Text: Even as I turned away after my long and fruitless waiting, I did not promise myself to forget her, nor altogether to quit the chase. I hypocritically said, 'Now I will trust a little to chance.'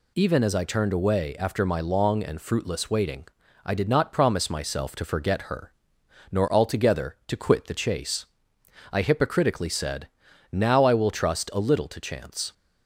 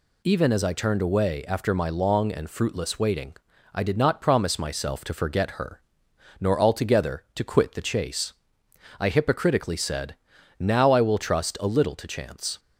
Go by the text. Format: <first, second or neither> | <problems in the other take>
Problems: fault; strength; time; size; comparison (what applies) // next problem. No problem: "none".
neither | none